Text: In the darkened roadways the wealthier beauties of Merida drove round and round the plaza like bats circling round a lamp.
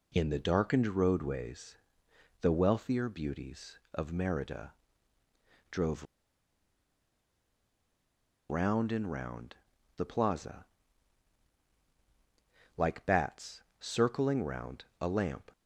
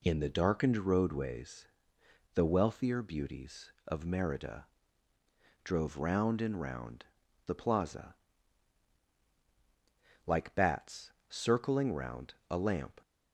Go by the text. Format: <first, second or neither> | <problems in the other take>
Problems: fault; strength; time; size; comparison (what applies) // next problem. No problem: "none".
second | pauses between "roadways" and "the"; noticeable; at 1.7 s; 0.62 s long; noticeable in the second // pauses between "Merida" and "drove"; noticeable; at 4.7 s; 0.96 s long; noticeable in the second // pauses between "drove" and "round"; strong; at 6.0 s; 2.4 s long // pauses between "round" and "the"; at 9.5 s; 0.40 s long; also in the second // pauses between "plaza" and "like"; strong; at 10.6 s; 2.1 s long; strong in the second // pauses between "bats" and "circling"; slight; at 13.6 s; 0.18 s long; slight in the second